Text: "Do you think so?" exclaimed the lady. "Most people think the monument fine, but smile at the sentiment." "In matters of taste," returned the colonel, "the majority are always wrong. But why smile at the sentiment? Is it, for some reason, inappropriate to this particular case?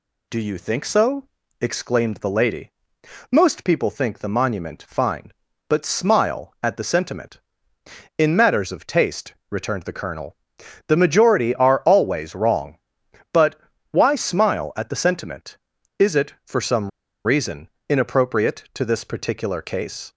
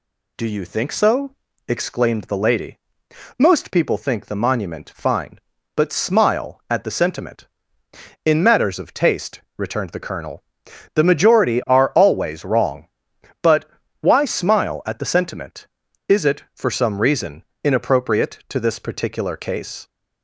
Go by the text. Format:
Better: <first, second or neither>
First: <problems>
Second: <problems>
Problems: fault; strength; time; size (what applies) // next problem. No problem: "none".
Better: second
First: pauses between "But" and "why"; slight; at 13.5 s; 0.32 s long // pauses between "some" and "reason"; at 16.8 s; 0.36 s long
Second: pauses between "But" and "why"; slight; at 13.6 s; 0.32 s long